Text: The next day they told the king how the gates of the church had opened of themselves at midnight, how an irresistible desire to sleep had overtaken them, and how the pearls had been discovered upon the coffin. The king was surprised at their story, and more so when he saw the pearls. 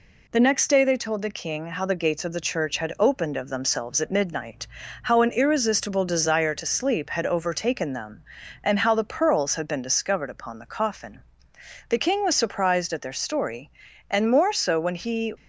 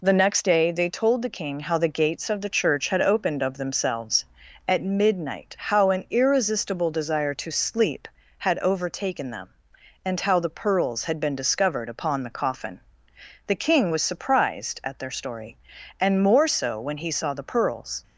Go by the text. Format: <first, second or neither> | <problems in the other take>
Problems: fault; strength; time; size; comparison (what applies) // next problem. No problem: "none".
second | stops before "saw the pearls"; at 15.3 s